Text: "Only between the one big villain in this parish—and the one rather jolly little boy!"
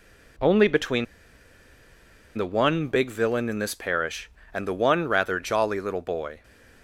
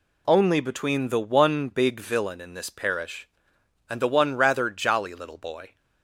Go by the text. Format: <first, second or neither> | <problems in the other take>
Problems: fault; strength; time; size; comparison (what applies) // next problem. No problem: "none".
second | pauses between "between" and "the"; strong; at 1.0 s; 1.3 s long